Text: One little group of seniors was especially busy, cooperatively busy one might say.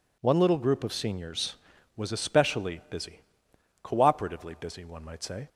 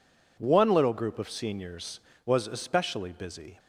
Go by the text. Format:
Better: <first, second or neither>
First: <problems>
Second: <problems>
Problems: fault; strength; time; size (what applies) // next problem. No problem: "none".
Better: first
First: none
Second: stops before "cooperatively busy one might say"; at 3.5 s